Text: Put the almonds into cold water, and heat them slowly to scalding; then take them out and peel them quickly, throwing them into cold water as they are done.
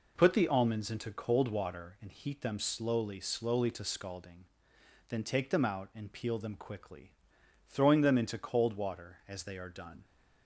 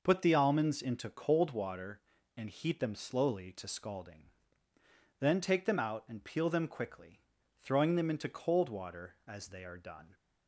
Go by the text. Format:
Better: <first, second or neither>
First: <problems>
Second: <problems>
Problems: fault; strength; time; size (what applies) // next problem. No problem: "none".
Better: second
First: says "slowly" twice; at 3.2 s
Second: none